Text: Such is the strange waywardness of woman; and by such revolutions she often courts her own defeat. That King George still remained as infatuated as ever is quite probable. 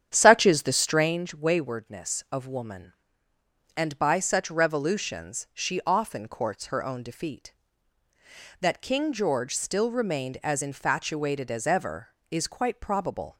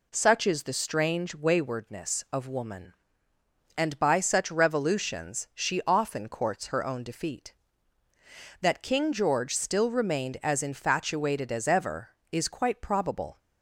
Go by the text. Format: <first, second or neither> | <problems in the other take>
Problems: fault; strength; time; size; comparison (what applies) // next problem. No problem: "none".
second | starts louder than the rest; strong; until 1.2 s; 8.5 dB